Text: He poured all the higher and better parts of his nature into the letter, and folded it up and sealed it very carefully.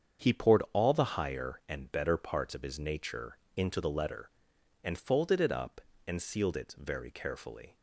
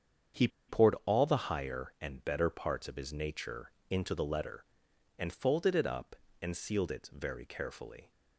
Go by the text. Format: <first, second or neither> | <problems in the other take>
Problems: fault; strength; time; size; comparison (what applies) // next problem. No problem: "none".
first | starts louder than the rest; strong; until 1.6 s; 7.5 dB; strong in the first // pauses between "He" and "poured"; slight; at 0.4 s; 0.19 s long // pauses between "nature" and "into"; slight; at 3.7 s; 0.18 s long; slight in the first